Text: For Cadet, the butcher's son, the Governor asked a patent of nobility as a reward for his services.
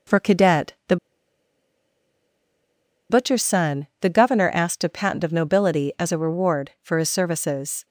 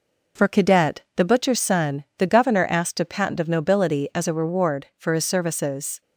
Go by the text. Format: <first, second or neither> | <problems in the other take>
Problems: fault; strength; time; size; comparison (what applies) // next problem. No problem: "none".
second | pauses between "the" and "butcher's"; strong; at 0.9 s; 2.1 s long